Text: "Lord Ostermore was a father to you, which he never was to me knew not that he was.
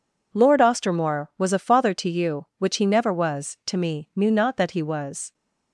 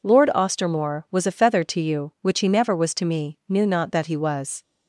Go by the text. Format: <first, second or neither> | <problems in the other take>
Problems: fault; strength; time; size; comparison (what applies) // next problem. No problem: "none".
first | says "feather" for "father"; at 1.3 s